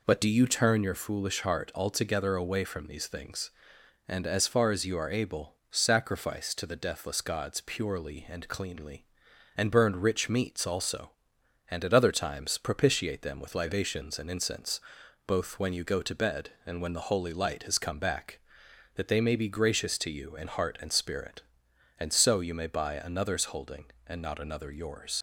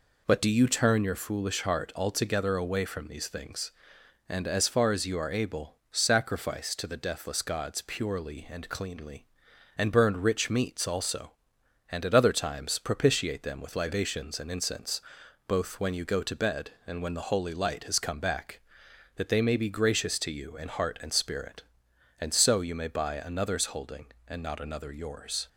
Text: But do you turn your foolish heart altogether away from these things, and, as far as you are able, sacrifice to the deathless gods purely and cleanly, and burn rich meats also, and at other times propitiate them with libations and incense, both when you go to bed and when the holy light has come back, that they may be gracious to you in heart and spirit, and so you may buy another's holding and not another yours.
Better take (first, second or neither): second